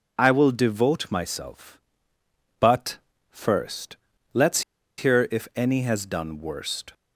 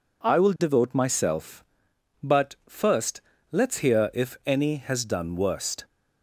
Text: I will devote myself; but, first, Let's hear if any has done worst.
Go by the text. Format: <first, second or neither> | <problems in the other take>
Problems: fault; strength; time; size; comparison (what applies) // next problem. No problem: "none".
second | pauses between "Let's" and "hear"; at 4.6 s; 0.37 s long